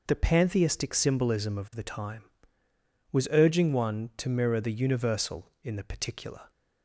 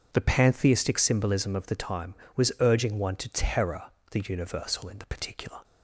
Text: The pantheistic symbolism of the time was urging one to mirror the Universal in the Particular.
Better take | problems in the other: first | says "terror" for "mirror"; at 3.3 s

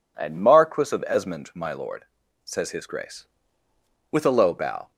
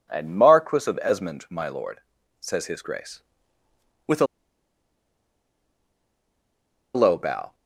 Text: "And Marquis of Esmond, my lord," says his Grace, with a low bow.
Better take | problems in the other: first | pauses between "a" and "low"; strong; at 4.2 s; 2.6 s long

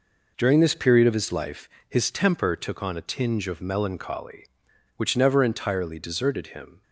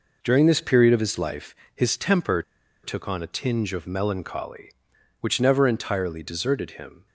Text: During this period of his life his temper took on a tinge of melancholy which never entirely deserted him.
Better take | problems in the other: first | pauses between "life" and "his"; slight; at 1.5 s; 0.20 s long; slight in the first // pauses between "temper" and "took"; at 2.4 s; 0.40 s long

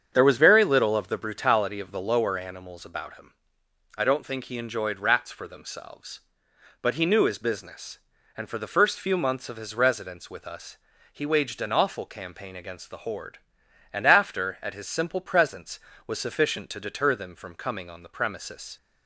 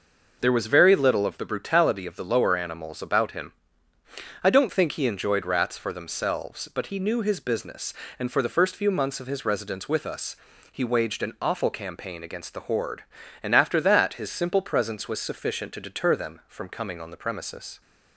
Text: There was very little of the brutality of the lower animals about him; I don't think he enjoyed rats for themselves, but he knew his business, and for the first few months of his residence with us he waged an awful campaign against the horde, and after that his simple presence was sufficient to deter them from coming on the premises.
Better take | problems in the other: second | starts louder than the rest; strong; until 1.1 s; 7.5 dB // pauses between "us" and "he"; at 10.7 s; 0.38 s long; slight in the second // says "at" for "that"; at 14.6 s

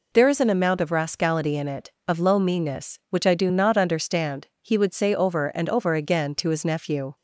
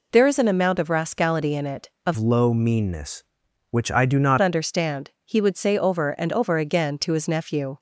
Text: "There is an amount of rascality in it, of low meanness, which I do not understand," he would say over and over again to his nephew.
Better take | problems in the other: first | changes voice from "low" to "not"; from 2.1 to 4.3 s; 2.2 s long

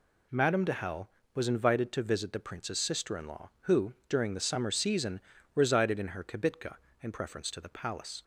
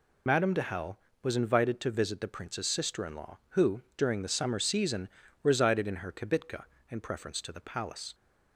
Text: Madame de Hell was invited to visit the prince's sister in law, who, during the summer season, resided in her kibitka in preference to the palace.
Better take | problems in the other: first | loses the start of "Madame"; at 0.2 s; 65 ms

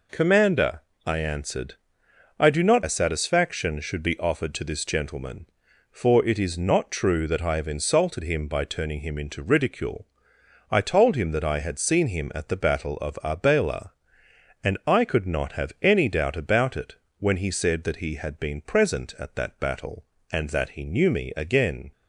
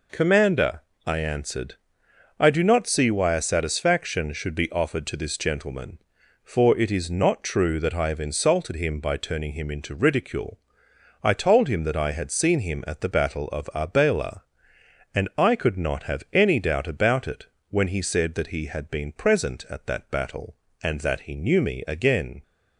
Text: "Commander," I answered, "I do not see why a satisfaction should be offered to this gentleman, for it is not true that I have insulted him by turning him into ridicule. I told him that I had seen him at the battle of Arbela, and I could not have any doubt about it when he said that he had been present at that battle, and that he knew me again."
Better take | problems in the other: second | skips "see why"; at 2.8 s // pauses between "it" and "when"; slight; at 16.9 s; 0.24 s long; slight in the second

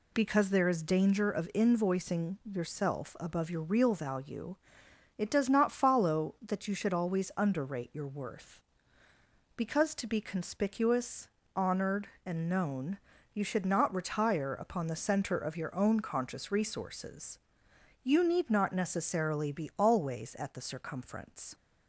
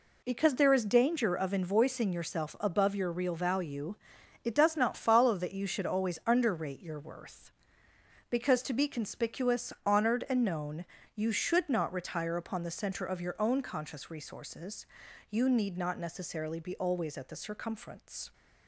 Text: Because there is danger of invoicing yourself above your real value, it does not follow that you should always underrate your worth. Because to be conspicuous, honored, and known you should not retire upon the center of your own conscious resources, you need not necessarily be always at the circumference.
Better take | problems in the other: neither | pauses between "known" and "you"; slight; the same in both

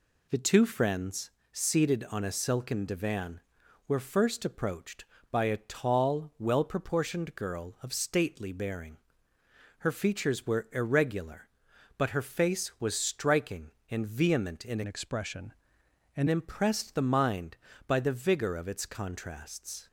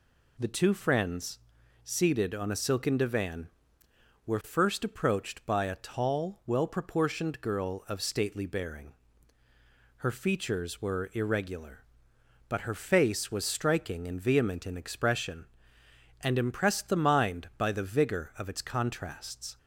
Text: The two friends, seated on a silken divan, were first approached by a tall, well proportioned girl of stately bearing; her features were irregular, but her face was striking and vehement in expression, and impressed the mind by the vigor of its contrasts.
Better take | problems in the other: second | changes voice from "expression" to "and"; from 14.8 to 16.2 s; 1.4 s long

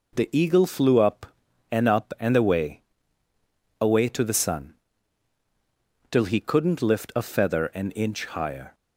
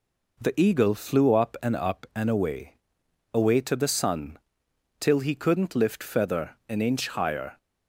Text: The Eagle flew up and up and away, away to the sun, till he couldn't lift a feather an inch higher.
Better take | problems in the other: first | skips "a"; at 6.0 s

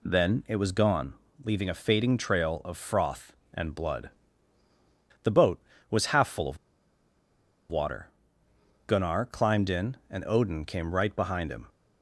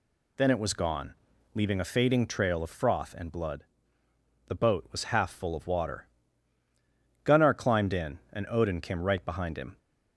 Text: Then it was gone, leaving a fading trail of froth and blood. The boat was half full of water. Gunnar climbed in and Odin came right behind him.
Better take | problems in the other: second | pauses between "of" and "water"; at 6.5 s; 1.1 s long

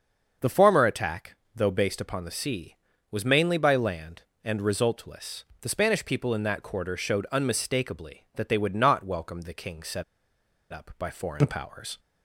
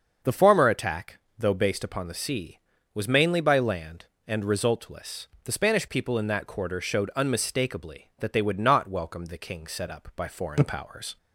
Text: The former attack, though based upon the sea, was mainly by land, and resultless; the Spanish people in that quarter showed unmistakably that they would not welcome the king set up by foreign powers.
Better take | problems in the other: second | starts louder than the rest; until 1.5 s; 6.5 dB; also in the second // pauses between "set" and "up"; noticeable; at 10.0 s; 0.69 s long

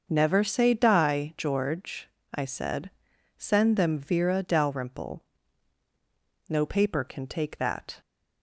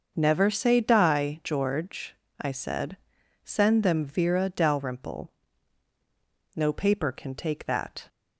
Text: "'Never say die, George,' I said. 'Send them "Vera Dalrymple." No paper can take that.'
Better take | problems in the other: neither | starts louder than the rest; the same in both

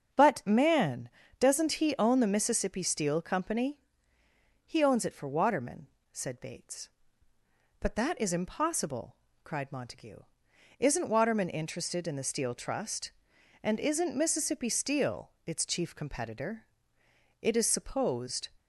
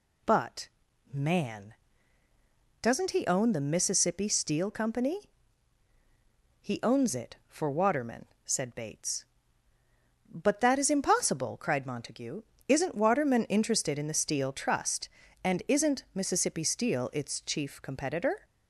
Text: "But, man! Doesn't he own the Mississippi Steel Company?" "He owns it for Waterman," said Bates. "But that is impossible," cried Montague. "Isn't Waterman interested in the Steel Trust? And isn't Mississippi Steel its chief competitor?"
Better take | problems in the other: second | starts louder than the rest; strong; until 1.5 s; 7.5 dB // goes on to say "It is supposed"; noticeable; from 17.3 s on; 1.1 s long

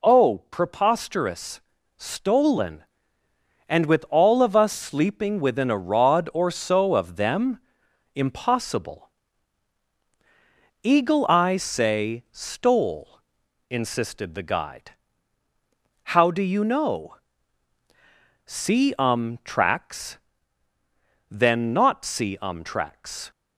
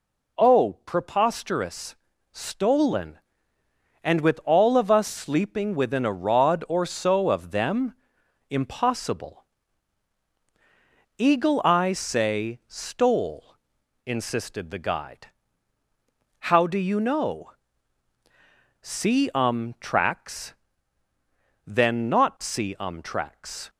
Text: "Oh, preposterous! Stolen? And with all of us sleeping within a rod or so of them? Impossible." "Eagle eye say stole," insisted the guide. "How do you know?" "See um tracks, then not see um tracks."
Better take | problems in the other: neither | none

